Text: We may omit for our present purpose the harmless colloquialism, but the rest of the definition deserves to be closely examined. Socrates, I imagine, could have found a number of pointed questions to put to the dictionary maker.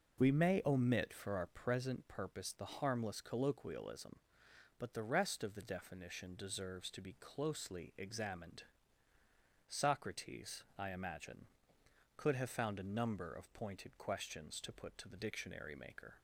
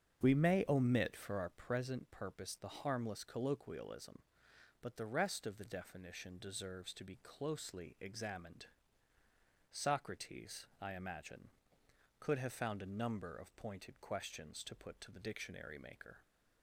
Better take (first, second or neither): first